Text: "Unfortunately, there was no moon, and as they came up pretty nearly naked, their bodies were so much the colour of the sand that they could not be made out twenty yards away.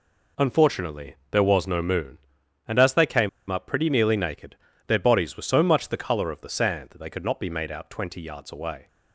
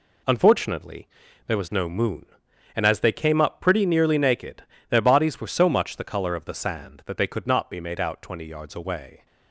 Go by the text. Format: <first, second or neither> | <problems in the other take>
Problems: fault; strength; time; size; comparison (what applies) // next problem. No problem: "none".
second | pauses between "came" and "up"; slight; at 3.2 s; 0.19 s long